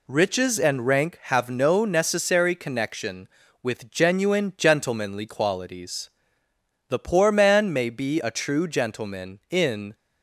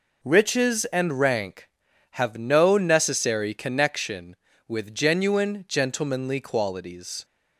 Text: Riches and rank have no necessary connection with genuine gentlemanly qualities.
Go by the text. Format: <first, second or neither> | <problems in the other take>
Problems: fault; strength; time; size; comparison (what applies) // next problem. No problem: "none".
second | goes on to say "The poor man may be a true gentleman in"; strong; from 6.8 s on; 3.0 s long